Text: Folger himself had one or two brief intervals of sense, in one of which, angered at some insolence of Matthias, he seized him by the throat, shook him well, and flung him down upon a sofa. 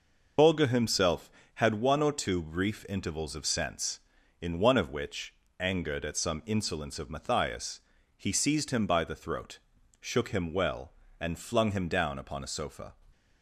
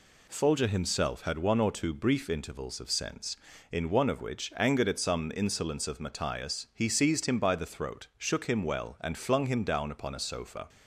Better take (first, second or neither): second